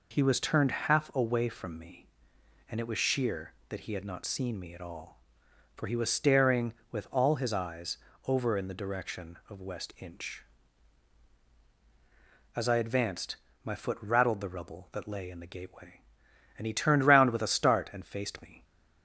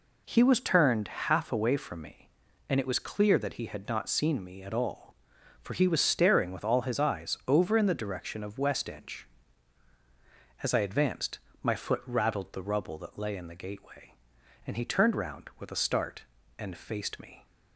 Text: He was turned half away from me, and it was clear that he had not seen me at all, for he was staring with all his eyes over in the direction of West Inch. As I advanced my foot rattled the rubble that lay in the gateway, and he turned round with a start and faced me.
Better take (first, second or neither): second